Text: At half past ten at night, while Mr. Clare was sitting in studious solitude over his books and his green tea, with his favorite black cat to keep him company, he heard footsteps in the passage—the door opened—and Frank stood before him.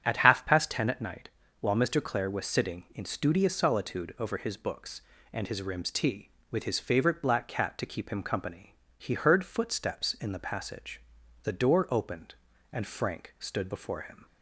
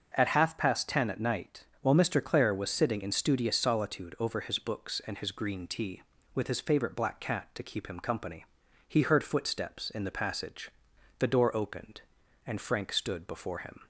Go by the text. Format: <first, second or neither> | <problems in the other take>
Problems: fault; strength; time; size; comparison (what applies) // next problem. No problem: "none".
second | starts louder than the rest; strong; until 1.0 s; 9 dB; noticeable in the second // says "rims" for "green"; at 5.6 s